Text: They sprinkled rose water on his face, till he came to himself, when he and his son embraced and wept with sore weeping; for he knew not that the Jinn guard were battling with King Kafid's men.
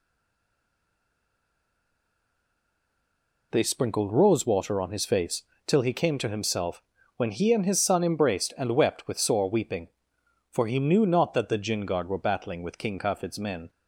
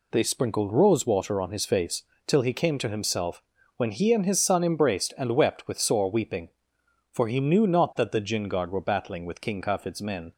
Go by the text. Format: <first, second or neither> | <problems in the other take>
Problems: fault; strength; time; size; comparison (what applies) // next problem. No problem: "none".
second | stays silent before the first word; strong; until 3.5 s; 3.5 s long